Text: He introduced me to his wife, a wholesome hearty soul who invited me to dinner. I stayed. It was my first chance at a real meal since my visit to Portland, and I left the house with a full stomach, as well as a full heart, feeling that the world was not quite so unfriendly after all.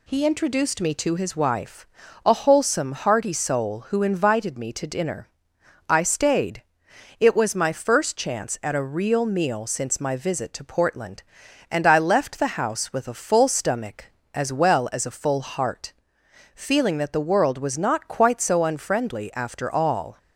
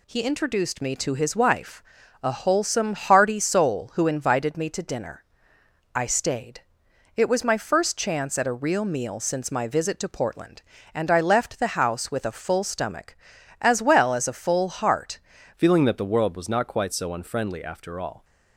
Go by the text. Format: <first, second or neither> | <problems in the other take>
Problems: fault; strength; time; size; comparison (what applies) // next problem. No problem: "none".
first | changes voice at "feeling"; from 15.5 s on; 2.7 s long